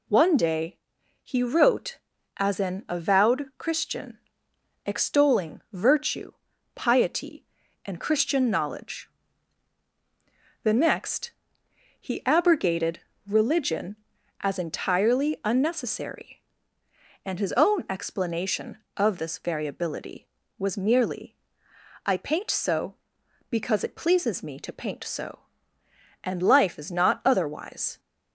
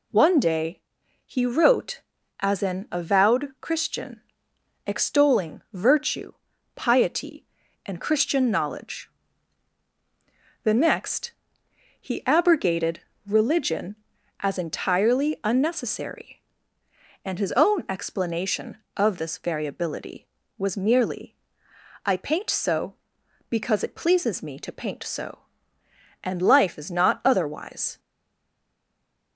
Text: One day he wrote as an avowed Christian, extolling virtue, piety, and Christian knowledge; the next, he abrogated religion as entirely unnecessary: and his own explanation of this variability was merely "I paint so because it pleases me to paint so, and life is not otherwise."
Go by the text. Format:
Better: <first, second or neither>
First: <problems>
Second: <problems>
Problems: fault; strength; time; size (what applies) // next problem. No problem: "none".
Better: first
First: pauses between "day" and "he"; noticeable; at 0.7 s; 0.46 s long // pauses between "abrogated" and "religion"; slight; at 12.9 s; 0.26 s long // pauses between "merely" and "I"; noticeable; at 21.3 s; 0.70 s long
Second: pauses between "day" and "he"; noticeable; at 0.7 s; 0.46 s long // pauses between "abrogated" and "religion"; slight; at 12.9 s; 0.25 s long // pauses between "merely" and "I"; noticeable; at 21.3 s; 0.70 s long // stays silent after the last word; noticeable; from 27.9 s on; 1.4 s long